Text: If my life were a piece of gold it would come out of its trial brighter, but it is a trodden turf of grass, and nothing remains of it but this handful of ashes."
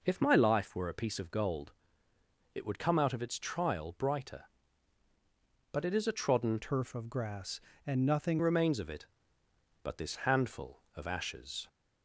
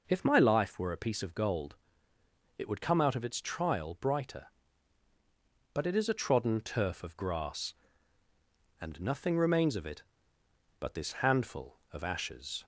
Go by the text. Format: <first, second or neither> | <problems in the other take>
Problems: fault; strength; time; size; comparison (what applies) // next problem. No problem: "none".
second | pauses between "gold" and "it"; noticeable; at 1.7 s; 0.82 s long; noticeable in the second // changes voice from "turf" to "nothing"; from 6.6 to 8.3 s; 1.7 s long